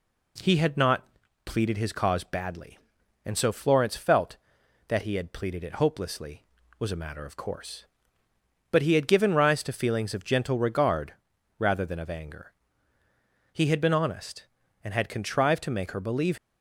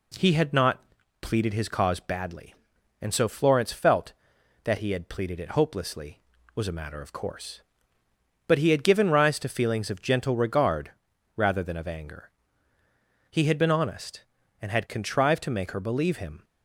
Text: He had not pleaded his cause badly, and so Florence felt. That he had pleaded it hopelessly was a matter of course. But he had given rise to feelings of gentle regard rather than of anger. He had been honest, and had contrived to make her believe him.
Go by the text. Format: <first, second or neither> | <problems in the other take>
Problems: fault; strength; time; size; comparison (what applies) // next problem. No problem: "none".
second | pauses between "not" and "pleaded"; at 1.0 s; 0.40 s long; also in the second // pauses between "regard" and "rather"; at 11.1 s; 0.42 s long; also in the second // stops before "him"; at 16.3 s